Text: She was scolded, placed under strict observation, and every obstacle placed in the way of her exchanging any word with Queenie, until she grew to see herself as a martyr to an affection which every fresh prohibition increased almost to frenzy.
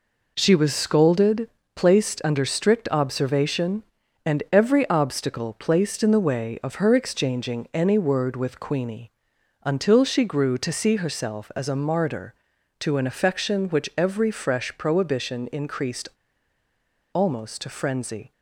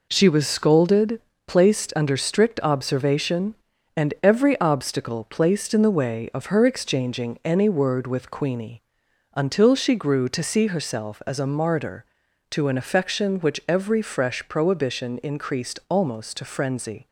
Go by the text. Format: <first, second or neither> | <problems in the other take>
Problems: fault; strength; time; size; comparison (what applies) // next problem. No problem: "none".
second | pauses between "increased" and "almost"; at 16.0 s; 1.0 s long